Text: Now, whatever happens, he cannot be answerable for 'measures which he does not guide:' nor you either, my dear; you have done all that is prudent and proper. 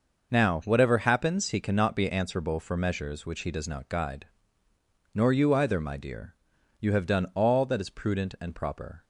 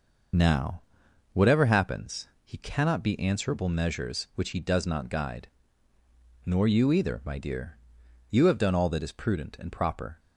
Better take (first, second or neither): first